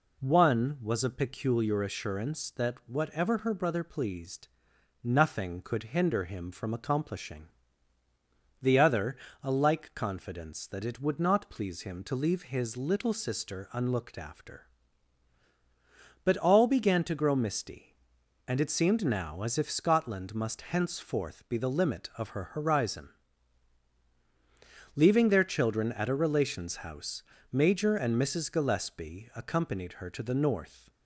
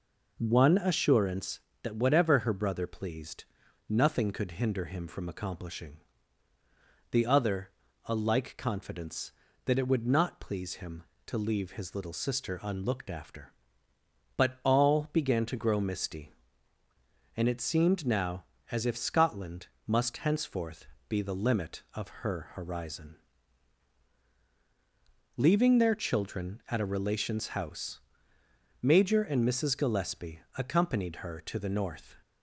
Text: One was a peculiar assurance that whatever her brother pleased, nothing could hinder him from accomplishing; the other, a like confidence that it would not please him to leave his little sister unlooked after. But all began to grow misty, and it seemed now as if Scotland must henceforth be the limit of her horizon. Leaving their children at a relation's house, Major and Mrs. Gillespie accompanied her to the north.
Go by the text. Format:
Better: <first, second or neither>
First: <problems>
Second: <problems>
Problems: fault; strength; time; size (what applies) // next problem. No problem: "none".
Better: first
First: none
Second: skips "was a peculiar"; at 0.7 s // pauses between "Scotland" and "must"; slight; at 19.6 s; 0.22 s long // pauses between "henceforth" and "be"; slight; at 20.8 s; 0.22 s long // pauses between "Gillespie" and "accompanied"; slight; at 30.3 s; 0.16 s long